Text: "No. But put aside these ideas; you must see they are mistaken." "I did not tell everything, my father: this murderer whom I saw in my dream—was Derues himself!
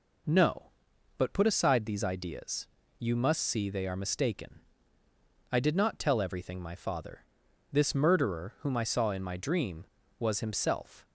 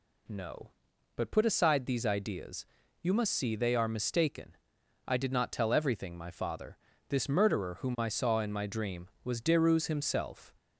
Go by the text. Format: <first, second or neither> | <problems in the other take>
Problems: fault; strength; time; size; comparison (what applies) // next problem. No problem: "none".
second | skips "Derues"; at 10.4 s